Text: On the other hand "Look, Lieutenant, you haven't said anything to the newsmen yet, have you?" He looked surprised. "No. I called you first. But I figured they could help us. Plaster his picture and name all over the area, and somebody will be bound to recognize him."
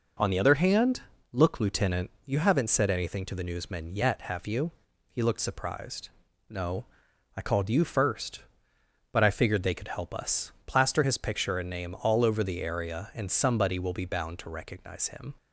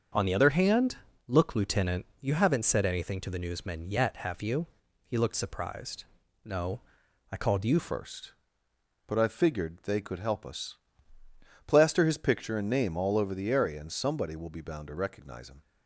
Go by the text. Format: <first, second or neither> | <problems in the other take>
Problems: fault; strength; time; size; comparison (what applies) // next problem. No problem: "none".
first | starts louder than the rest; until 1.4 s; 7 dB // pauses between "hand" and "Look"; slight; at 0.9 s; 0.30 s long; slight in the first // changes voice at "first"; from 7.7 s on; 7.9 s long